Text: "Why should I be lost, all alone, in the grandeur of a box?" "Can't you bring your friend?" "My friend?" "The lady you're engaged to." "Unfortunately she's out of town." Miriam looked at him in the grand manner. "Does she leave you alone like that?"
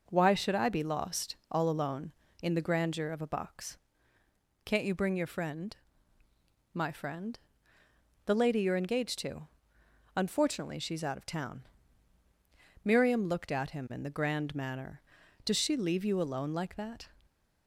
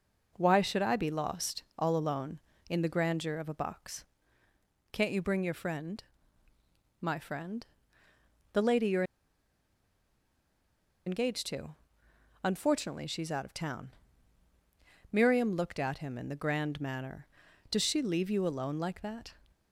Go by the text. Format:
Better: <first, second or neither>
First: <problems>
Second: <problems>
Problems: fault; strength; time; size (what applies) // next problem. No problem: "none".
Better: first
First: none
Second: pauses between "you're" and "engaged"; strong; at 9.0 s; 2.0 s long